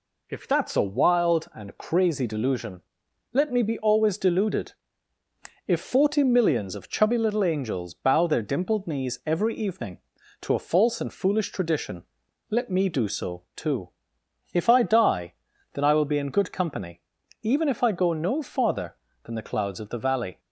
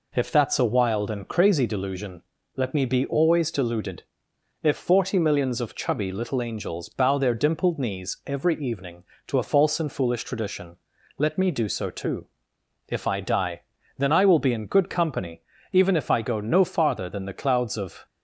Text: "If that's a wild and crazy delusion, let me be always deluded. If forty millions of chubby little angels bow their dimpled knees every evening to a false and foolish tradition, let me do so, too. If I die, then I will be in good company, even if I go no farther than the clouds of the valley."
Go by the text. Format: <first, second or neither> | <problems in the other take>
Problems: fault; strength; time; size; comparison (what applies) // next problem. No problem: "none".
first | stops before "the valley"; at 18.0 s